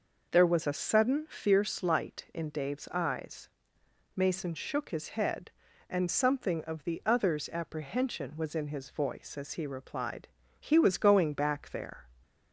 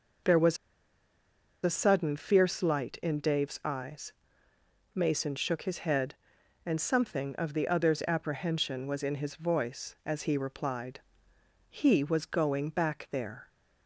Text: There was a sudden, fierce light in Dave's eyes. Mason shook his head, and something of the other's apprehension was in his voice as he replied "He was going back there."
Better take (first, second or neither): first